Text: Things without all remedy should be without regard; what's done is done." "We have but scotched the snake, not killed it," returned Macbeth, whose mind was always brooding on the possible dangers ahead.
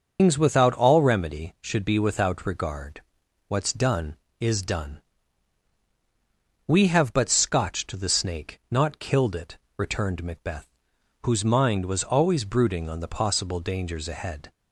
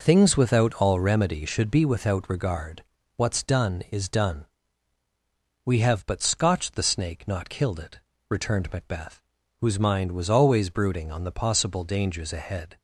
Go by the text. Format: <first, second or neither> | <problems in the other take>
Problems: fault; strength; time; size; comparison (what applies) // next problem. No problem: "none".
second | loses the start of "Things"; at 0.1 s; 170 ms // starts louder than the rest; until 1.2 s; 6.5 dB